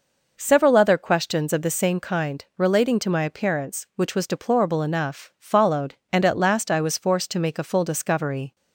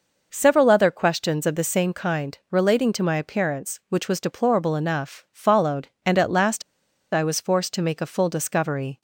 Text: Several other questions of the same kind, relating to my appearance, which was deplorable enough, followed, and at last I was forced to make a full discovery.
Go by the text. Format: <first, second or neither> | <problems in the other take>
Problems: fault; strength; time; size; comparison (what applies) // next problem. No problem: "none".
first | pauses between "last" and "I"; noticeable; at 6.6 s; 0.50 s long